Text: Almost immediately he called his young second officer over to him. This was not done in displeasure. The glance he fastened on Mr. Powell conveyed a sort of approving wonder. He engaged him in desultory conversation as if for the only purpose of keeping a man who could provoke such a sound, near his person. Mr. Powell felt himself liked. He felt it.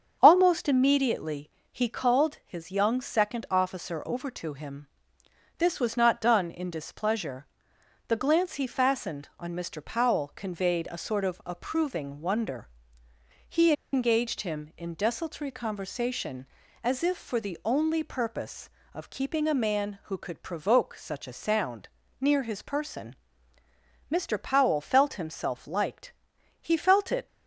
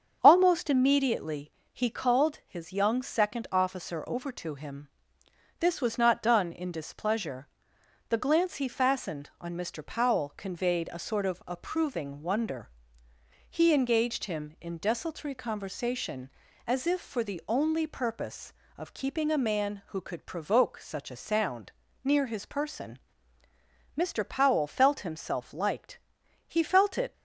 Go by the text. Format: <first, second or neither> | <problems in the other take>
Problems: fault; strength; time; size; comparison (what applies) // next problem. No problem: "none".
second | starts louder than the rest; strong; until 1.2 s; 7.5 dB; strong in the second // pauses between "immediately" and "he"; slight; at 1.5 s; 0.20 s long; slight in the second // pauses between "He" and "engaged"; slight; at 13.7 s; 0.20 s long